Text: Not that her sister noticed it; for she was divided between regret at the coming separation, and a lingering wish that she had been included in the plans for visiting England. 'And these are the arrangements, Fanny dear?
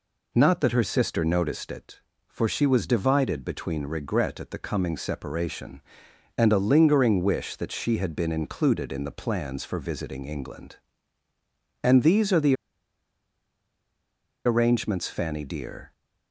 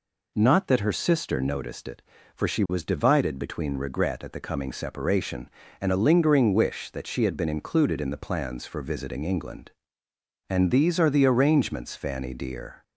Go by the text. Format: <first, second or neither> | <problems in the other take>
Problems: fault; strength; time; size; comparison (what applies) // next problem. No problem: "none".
second | pauses between "the" and "arrangements"; strong; at 12.5 s; 1.9 s long